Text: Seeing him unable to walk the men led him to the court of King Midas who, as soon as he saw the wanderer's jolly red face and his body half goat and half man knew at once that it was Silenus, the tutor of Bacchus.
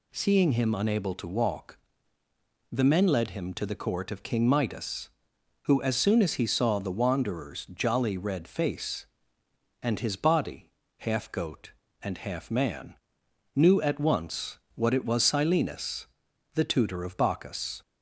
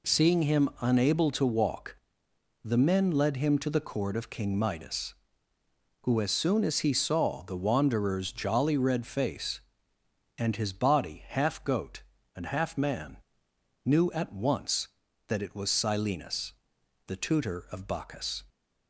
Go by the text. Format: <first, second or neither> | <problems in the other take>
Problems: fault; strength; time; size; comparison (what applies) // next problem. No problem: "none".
second | pauses between "walk" and "the"; noticeable; at 1.7 s; 0.92 s long; noticeable in the second // pauses between "body" and "half"; slight; at 10.6 s; 0.30 s long // pauses between "man" and "knew"; noticeable; at 12.9 s; 0.60 s long; noticeable in the second // says "what" for "that"; at 14.7 s